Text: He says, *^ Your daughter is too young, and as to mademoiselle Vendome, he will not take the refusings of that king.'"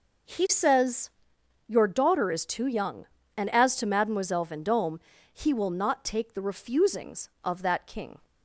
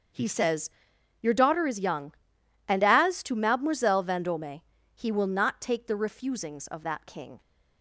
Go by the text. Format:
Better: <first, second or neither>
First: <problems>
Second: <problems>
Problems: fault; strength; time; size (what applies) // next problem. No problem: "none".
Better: first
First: none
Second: starts louder than the rest; until 1.6 s; 6.5 dB // skips "too"; at 1.7 s